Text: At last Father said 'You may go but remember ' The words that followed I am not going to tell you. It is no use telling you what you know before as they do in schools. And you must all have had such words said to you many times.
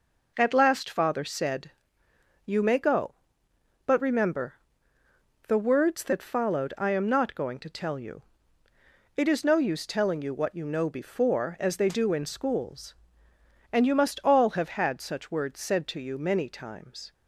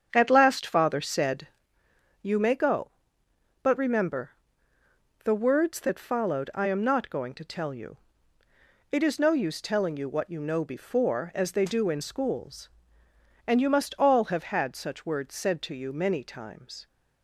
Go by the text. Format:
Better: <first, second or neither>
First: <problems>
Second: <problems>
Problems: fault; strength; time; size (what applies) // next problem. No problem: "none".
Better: first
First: pauses between "said" and "You"; noticeable; at 1.6 s; 0.74 s long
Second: starts louder than the rest; strong; until 1.7 s; 8 dB // pauses between "said" and "You"; noticeable; at 1.4 s; 0.74 s long